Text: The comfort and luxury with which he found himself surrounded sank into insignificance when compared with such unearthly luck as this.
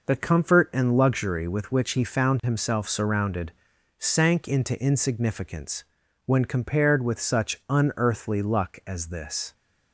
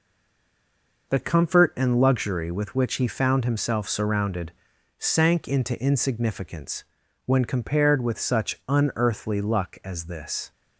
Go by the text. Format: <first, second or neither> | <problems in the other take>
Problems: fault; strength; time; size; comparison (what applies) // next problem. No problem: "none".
first | stays silent before the first word; until 1.0 s; 1.0 s long // pauses between "surrounded" and "sank"; noticeable; at 4.5 s; 0.46 s long; noticeable in the first // pauses between "insignificance" and "when"; at 6.8 s; 0.40 s long; also in the first